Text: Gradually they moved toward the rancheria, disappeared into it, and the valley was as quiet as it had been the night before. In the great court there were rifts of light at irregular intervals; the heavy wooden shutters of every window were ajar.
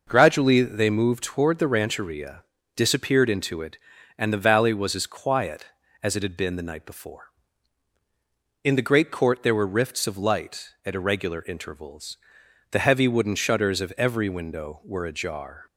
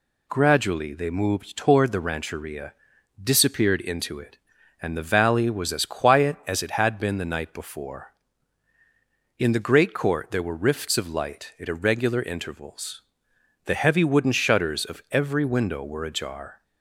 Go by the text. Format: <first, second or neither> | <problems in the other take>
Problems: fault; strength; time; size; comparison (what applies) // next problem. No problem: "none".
neither | none